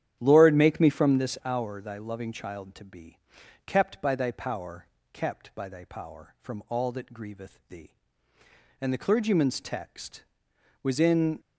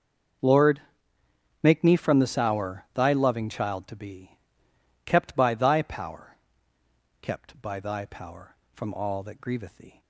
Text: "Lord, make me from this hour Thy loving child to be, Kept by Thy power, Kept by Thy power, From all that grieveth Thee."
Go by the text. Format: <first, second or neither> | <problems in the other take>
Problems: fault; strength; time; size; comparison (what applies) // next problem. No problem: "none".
second | starts louder than the rest; strong; until 1.2 s; 10 dB; also in the second // goes on to say "And the clergyman's text was in"; strong; from 8.7 s on; 2.6 s long